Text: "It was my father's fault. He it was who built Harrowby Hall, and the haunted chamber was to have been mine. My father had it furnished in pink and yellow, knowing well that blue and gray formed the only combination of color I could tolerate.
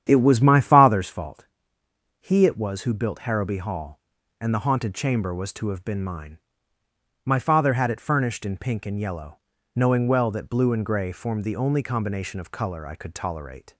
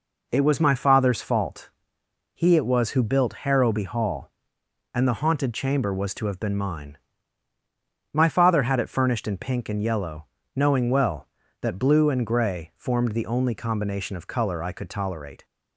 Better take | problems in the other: second | starts louder than the rest; strong; until 1.1 s; 9.5 dB

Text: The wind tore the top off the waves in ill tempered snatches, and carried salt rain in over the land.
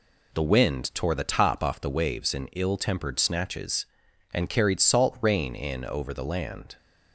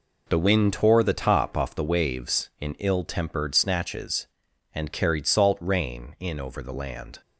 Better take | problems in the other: neither | none

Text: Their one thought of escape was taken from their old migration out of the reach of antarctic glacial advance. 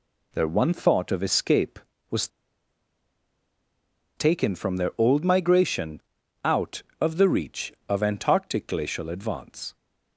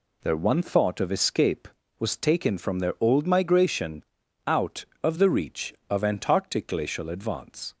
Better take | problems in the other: second | pauses between "was" and "taken"; strong; at 2.2 s; 1.8 s long // pauses between "migration" and "out"; at 6.0 s; 0.42 s long; also in the second

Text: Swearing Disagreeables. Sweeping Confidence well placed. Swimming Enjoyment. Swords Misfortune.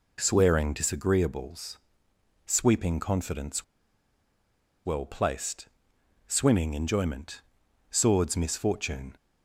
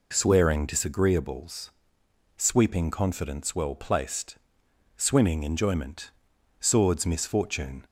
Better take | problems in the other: second | pauses between "Confidence" and "well"; at 3.6 s; 1.2 s long

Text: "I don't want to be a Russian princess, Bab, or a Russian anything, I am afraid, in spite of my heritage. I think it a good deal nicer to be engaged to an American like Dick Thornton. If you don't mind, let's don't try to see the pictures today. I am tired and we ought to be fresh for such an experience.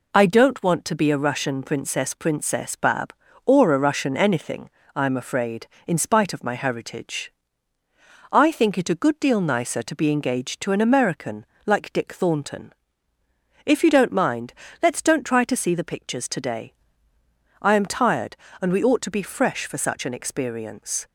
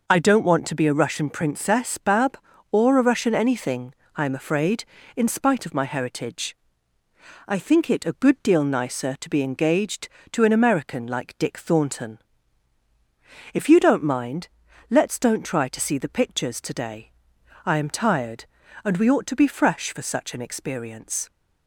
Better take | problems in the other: second | says "princess" twice; at 2.1 s // pauses between "American" and "like"; slight; at 11.4 s; 0.22 s long

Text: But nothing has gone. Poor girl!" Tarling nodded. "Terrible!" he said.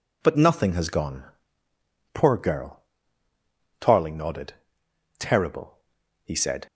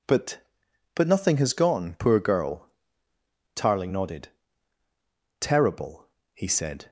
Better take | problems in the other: first | says "But" twice; at 0.9 s

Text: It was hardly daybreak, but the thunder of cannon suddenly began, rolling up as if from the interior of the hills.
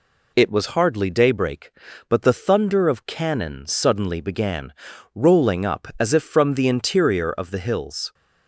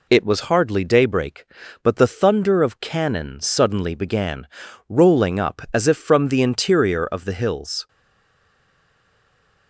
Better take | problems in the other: first | stays silent after the last word; noticeable; from 7.8 s on; 1.8 s long

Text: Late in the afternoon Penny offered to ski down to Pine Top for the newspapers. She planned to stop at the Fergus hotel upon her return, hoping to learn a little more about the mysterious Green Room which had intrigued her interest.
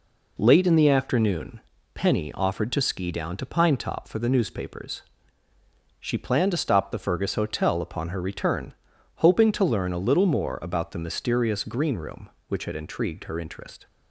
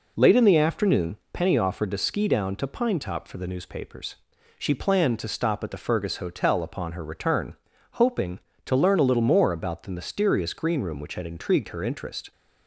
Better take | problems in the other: second | pauses between "afternoon" and "Penny"; slight; at 1.6 s; 0.34 s long; slight in the second // skips "at"; at 6.9 s

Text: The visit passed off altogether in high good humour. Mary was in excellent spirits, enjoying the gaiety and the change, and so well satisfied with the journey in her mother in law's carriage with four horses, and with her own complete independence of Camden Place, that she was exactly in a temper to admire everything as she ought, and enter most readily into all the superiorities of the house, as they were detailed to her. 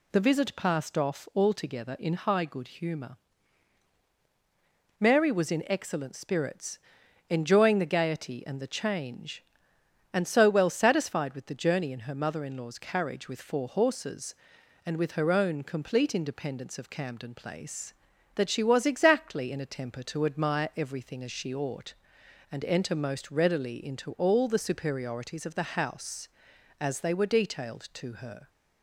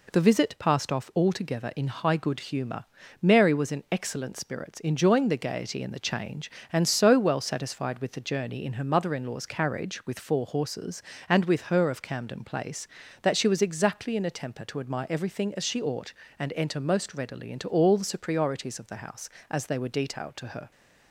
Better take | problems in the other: first | skips "own complete independence"; at 11.9 s

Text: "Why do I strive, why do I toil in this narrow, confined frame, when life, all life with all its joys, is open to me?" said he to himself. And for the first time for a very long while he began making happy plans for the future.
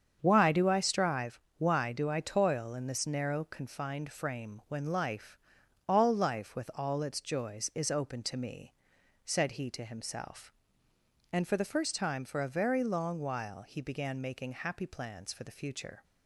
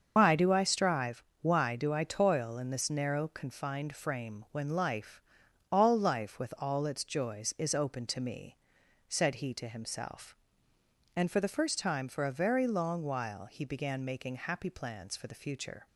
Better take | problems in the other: first | loses the start of "Why"; at 0.1 s; 115 ms // starts louder than the rest; until 1.1 s; 7 dB; strong in the first

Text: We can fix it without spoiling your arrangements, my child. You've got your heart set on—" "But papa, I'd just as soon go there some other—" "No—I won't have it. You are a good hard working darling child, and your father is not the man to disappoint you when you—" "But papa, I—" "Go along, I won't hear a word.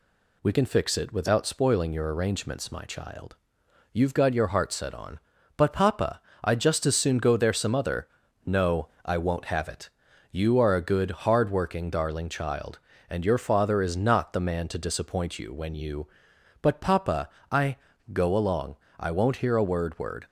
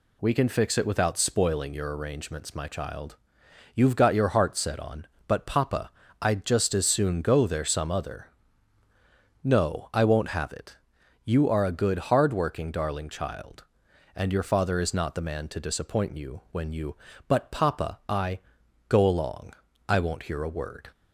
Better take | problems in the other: second | pauses between "good" and "hard"; slight; at 11.1 s; 0.16 s long // says "word" twice; at 19.9 s

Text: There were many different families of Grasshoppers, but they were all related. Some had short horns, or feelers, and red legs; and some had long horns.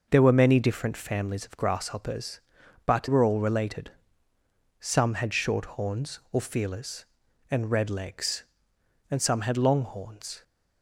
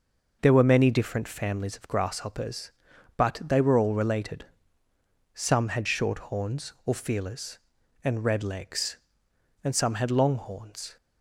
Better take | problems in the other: second | skips "they"; at 3.0 s

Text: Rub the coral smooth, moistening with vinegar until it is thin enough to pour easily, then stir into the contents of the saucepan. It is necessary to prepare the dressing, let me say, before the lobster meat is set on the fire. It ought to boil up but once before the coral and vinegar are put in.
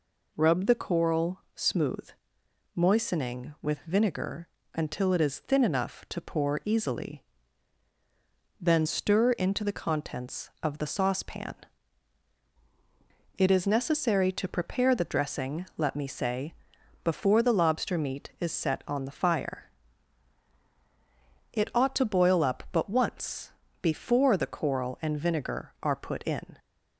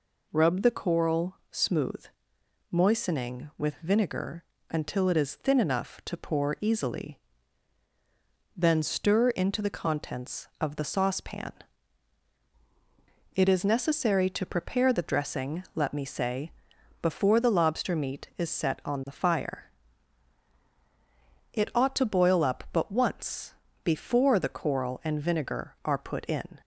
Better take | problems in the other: neither | pauses between "vinegar" and "until"; slight; the same in both // pauses between "once" and "before"; slight; the same in both

